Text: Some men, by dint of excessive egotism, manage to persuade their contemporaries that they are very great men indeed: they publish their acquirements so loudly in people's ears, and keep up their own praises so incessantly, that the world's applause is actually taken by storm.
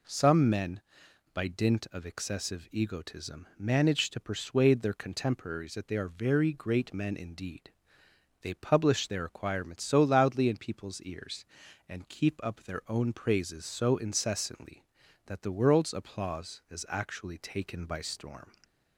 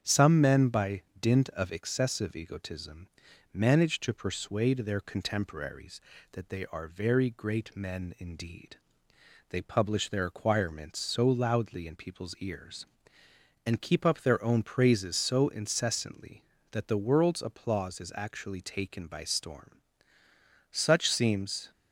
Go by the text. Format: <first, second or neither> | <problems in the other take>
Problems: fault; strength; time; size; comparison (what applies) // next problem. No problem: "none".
first | starts louder than the rest; strong; until 1.0 s; 8 dB // pauses between "by" and "dint"; slight; at 1.0 s; 0.18 s long // goes on to say "Such seems"; noticeable; from 20.7 s on; 1.0 s long